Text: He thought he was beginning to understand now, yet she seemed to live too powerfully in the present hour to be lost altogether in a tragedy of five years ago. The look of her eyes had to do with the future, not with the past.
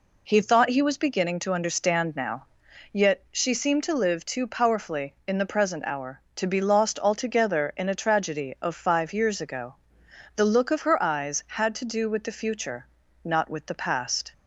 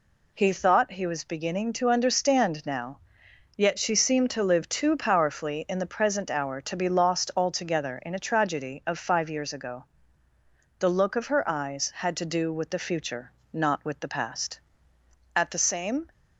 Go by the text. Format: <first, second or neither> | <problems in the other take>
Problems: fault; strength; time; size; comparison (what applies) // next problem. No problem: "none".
first | goes on to say "At the same"; noticeable; from 15.3 s on; 0.74 s long